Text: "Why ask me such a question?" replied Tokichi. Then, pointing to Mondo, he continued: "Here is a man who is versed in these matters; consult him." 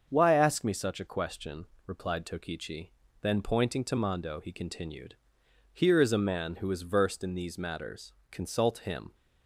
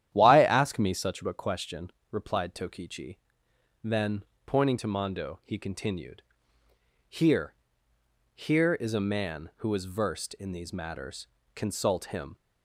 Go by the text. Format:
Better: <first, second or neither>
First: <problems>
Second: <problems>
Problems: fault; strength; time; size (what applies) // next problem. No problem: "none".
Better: first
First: starts louder than the rest; until 1.1 s; 6.5 dB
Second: starts louder than the rest; strong; until 1.1 s; 11 dB // says "Here" twice; at 8.3 s